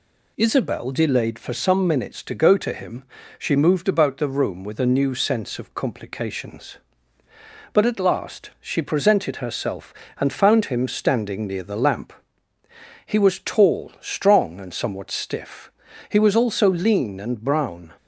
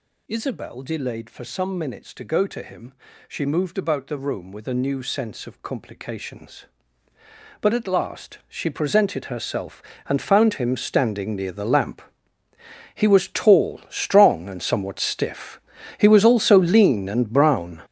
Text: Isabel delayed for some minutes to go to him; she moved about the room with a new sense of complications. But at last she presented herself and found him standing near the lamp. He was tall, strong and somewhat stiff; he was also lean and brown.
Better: first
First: none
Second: gets louder; strong; throughout; 11 dB

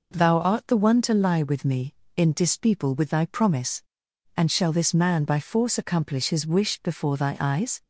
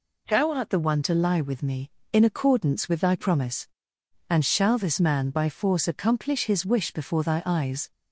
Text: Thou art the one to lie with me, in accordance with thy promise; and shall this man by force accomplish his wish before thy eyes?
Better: second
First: says "dispeople" for "accordance"; at 2.3 s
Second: none

